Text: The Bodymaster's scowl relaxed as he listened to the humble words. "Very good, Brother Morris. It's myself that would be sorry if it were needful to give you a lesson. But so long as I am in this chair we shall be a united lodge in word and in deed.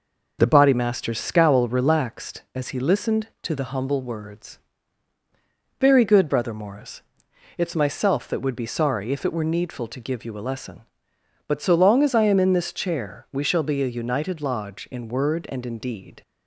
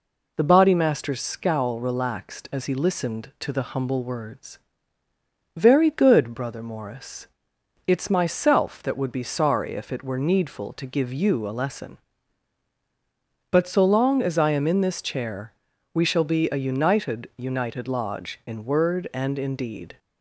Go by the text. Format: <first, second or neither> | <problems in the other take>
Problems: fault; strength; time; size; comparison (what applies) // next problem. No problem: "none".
first | pauses between "chair" and "we"; at 15.5 s; 0.40 s long // says "united" twice; at 17.3 s